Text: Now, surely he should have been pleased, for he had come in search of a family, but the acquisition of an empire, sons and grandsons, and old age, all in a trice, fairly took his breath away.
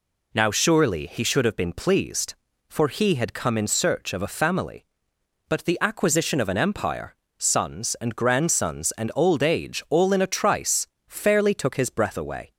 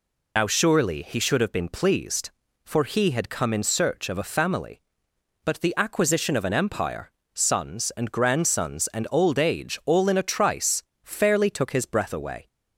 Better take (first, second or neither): first